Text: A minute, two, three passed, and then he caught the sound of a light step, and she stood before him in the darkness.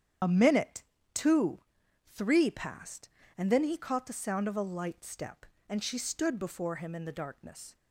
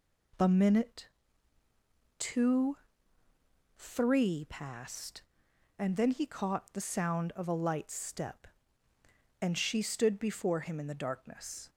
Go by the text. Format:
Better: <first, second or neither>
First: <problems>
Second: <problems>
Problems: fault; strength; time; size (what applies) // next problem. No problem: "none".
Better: second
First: loses the start of "A"; at 0.2 s; 40 ms // starts louder than the rest; strong; until 1.5 s; 8.5 dB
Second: none